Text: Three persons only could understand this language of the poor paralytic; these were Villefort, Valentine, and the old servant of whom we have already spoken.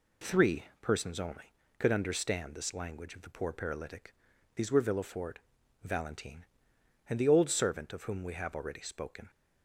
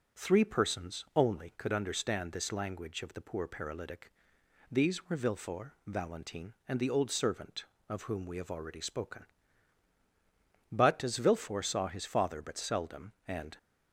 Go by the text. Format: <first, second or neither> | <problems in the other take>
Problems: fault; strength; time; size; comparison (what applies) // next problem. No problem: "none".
first | goes on to say "But as Villefort saw his father but seldom and"; strong; from 10.7 s on; 2.8 s long